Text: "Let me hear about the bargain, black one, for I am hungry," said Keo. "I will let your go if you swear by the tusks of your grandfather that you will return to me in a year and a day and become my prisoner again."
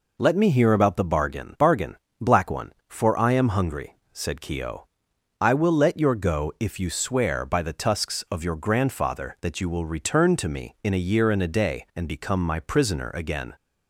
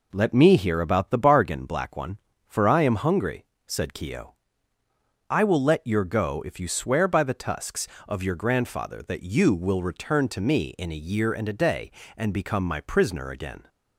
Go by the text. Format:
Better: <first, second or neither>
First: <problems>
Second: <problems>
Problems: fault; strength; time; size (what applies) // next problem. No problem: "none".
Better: second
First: says "bargain" twice; at 1.5 s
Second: none